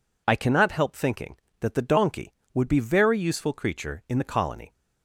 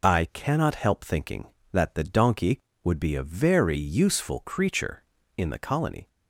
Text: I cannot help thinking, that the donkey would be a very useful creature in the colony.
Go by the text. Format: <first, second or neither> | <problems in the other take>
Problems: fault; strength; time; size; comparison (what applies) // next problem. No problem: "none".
second | skips "a"; at 2.7 s